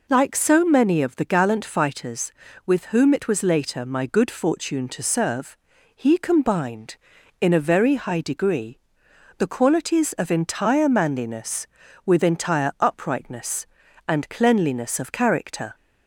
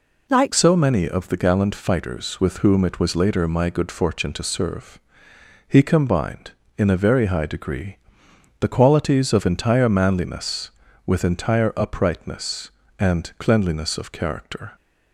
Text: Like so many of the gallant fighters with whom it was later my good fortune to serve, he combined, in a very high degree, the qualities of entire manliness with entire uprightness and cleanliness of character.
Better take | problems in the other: first | changes voice at "so"; from 0.5 s on; 14.2 s long

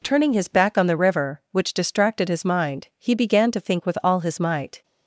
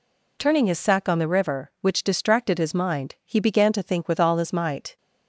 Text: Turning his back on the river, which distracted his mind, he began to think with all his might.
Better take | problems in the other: first | says "sack" for "back"; at 0.7 s

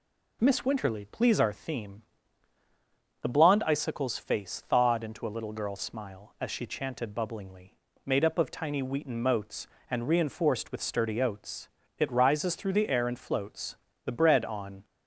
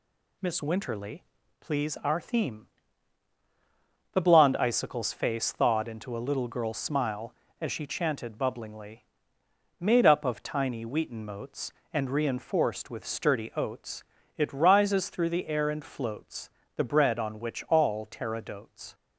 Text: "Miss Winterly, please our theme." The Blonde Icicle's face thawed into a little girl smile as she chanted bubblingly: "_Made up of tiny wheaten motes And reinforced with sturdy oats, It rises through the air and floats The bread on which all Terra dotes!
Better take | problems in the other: second | pauses between "floats" and "The"; slight; at 13.7 s; 0.30 s long; slight in the second // stops before "which all Terra dotes"; at 14.8 s

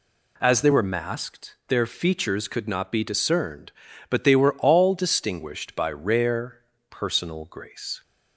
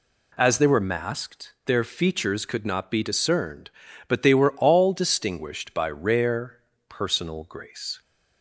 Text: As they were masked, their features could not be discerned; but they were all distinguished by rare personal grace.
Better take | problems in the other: neither | pauses between "rare" and "personal"; slight; the same in both

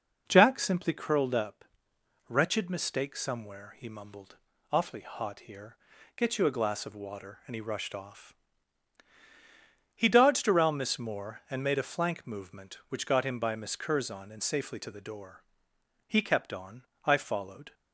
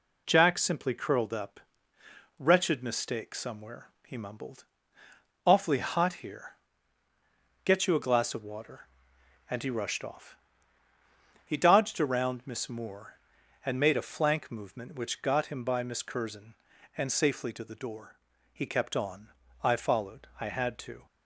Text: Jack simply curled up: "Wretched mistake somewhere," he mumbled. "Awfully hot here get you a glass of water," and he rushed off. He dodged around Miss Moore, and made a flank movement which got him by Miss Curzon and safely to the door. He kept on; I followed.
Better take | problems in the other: first | pauses between "here" and "get"; at 6.5 s; 1.1 s long; also in the first // goes on to say "I had to"; noticeable; from 20.3 s on; 0.66 s long

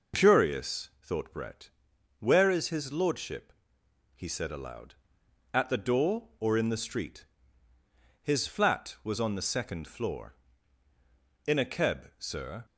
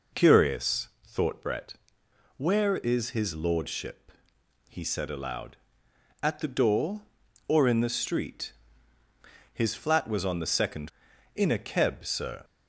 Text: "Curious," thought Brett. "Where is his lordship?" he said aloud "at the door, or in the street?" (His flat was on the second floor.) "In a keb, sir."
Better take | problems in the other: first | skips "floor"; at 11.1 s

